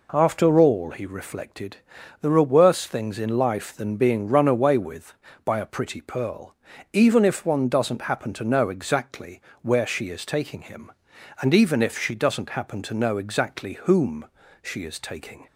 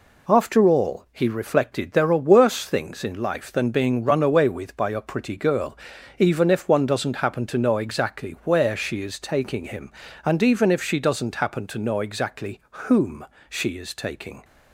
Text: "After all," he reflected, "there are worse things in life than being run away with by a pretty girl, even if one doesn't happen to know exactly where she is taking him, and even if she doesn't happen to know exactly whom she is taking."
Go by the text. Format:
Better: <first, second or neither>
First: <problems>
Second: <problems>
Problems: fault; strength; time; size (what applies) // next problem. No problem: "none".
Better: second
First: says "pearl" for "girl"; at 6.0 s // pauses between "exactly" and "where"; slight; at 9.4 s; 0.22 s long // pauses between "whom" and "she"; at 14.2 s; 0.38 s long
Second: pauses between "whom" and "she"; slight; at 13.2 s; 0.24 s long